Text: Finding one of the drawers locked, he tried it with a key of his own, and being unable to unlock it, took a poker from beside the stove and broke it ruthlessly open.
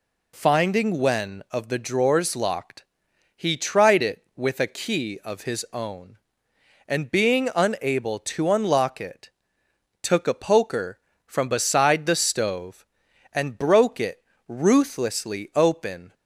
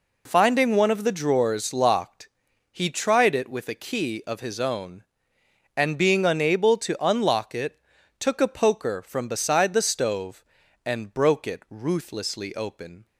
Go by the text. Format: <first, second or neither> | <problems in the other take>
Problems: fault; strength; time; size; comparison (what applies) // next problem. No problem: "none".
second | says "when" for "one"; at 0.9 s // pauses between "it" and "ruthlessly"; slight; at 14.2 s; 0.24 s long